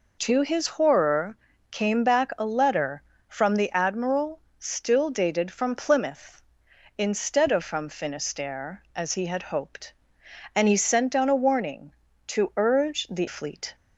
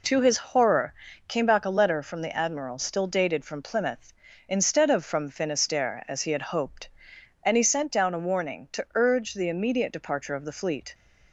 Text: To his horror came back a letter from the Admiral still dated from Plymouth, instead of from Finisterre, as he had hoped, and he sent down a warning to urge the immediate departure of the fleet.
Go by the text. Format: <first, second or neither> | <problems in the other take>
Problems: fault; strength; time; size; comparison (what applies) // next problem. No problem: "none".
second | pauses between "horror" and "came"; slight; at 1.3 s; 0.32 s long; slight in the second // pauses between "Admiral" and "still"; slight; at 4.3 s; 0.18 s long // skips "immediate departure of the"; at 13.2 s